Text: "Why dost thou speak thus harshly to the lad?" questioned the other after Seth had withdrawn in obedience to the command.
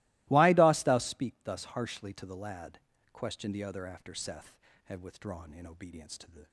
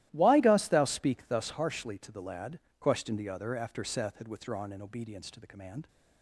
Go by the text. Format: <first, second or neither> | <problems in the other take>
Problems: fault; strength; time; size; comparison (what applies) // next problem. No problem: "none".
second | starts louder than the rest; strong; until 1.2 s; 21 dB; strong in the second // stops before "command"; at 6.4 s